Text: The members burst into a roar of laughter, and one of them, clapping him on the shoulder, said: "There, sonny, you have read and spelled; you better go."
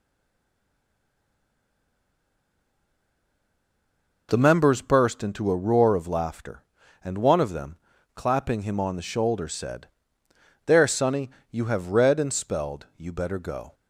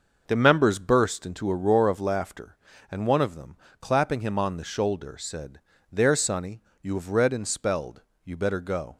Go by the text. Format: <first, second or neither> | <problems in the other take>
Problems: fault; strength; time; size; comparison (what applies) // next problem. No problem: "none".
second | stays silent before the first word; strong; until 4.2 s; 4.2 s long